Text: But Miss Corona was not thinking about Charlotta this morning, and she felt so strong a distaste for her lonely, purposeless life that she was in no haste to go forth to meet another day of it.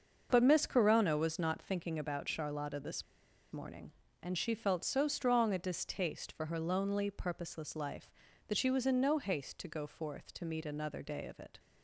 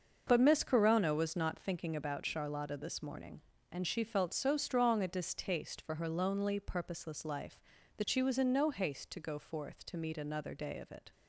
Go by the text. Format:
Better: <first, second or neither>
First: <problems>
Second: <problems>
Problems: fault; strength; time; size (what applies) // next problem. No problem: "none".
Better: second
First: starts louder than the rest; until 1.3 s; 6.5 dB // pauses between "this" and "morning"; noticeable; at 3.0 s; 0.49 s long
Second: starts louder than the rest; until 1.2 s; 6.5 dB